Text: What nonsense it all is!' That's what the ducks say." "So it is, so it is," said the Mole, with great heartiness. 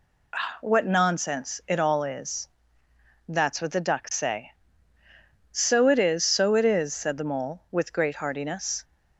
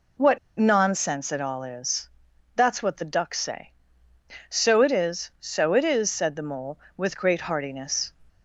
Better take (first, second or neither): first